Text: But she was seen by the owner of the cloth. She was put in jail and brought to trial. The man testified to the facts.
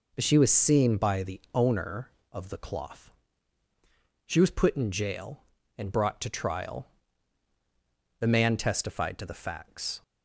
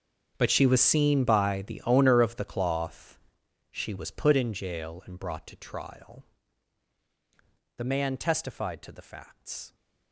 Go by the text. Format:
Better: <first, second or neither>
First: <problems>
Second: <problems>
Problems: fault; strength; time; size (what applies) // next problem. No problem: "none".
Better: first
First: none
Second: gets quieter; strong; throughout; 18 dB